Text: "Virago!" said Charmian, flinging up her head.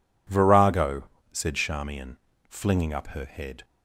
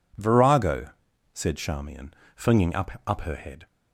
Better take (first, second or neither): first